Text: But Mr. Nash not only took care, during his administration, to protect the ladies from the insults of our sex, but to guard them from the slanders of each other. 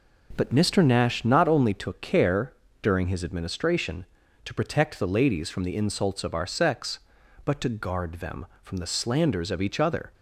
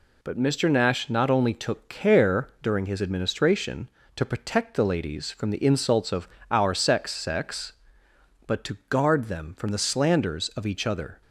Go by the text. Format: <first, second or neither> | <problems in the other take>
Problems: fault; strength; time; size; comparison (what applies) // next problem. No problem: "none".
first | pauses between "of" and "our"; slight; at 6.2 s; 0.24 s long // says "sex" twice; at 7.1 s